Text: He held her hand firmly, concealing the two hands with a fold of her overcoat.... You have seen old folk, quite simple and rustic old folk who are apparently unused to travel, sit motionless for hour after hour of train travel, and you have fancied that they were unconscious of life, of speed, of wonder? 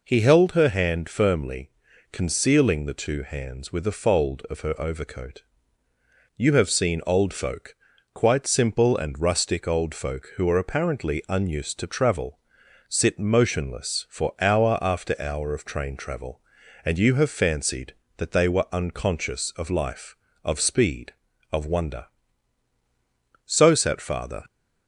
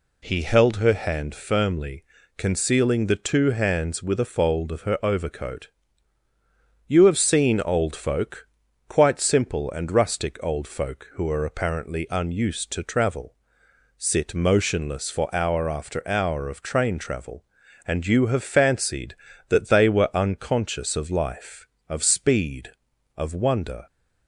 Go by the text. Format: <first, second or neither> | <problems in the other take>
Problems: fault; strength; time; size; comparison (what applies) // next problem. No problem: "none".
second | goes on to say "So sat Father"; noticeable; from 23.4 s on; 1.0 s long